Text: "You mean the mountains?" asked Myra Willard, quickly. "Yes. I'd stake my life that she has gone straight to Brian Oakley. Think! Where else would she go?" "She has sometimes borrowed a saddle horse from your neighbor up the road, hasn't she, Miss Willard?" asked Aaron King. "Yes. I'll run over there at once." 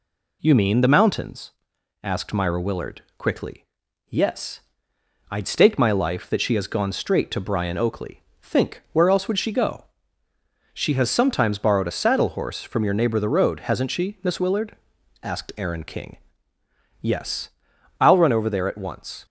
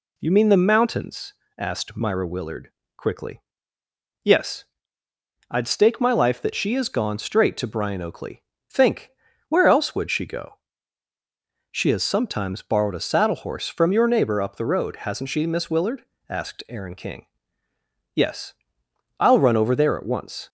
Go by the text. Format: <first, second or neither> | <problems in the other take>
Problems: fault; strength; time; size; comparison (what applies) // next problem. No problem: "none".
second | skips "up"; at 13.1 s